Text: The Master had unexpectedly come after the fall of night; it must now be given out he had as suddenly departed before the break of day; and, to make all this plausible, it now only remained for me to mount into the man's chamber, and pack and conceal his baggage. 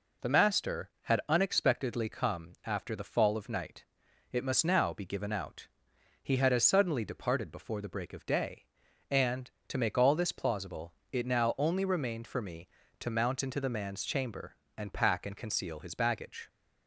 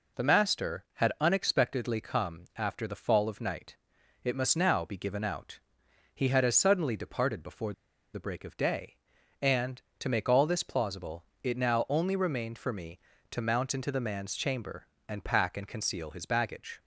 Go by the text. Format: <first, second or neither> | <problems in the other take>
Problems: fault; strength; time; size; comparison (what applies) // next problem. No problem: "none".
first | pauses between "out" and "he"; noticeable; at 5.5 s; 0.56 s long; noticeable in the first // pauses between "before" and "the"; at 7.7 s; 0.41 s long